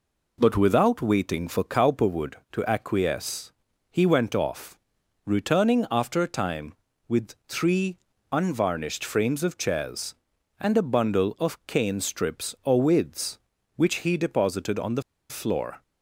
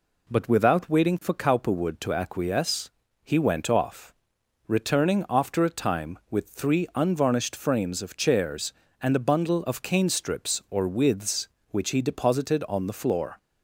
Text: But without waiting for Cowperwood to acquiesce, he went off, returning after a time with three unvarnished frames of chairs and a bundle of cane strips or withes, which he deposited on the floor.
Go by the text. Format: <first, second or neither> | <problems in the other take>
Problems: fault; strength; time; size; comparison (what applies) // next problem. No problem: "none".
second | pauses between "three" and "unvarnished"; slight; at 7.9 s; 0.34 s long // pauses between "the" and "floor"; slight; at 15.0 s; 0.27 s long